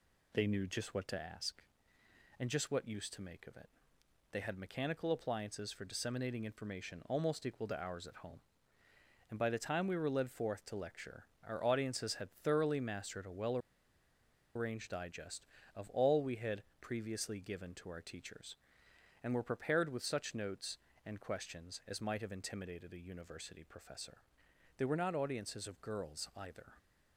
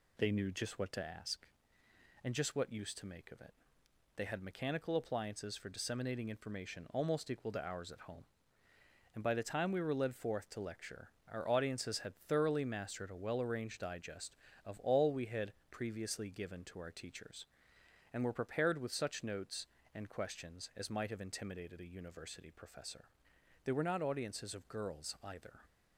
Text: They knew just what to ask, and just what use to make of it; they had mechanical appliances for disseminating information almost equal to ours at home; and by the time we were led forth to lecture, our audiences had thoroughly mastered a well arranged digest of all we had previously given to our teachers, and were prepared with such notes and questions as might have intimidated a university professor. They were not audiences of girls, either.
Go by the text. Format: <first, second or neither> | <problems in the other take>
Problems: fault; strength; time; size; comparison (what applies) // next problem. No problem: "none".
second | pauses between "well" and "arranged"; noticeable; at 13.5 s; 0.96 s long // pauses between "had" and "previously"; slight; at 16.6 s; 0.16 s long; slight in the second